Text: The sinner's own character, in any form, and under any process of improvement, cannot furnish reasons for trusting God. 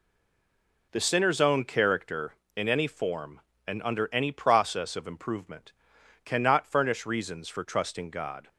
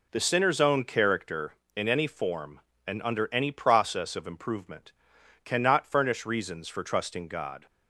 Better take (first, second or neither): second